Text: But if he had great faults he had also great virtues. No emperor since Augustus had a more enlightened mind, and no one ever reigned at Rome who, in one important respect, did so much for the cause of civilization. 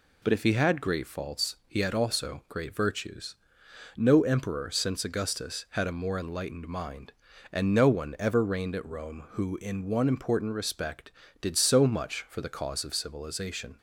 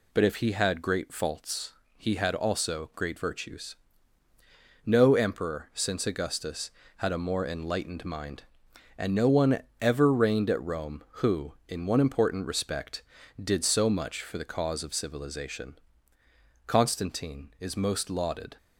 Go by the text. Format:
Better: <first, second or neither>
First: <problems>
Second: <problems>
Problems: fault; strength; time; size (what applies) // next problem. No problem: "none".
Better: first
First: none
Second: pauses between "faults" and "he"; slight; at 1.7 s; 0.24 s long // pauses between "one" and "ever"; slight; at 9.6 s; 0.22 s long // goes on to say "Constantine is most lauded"; strong; from 16.7 s on; 1.7 s long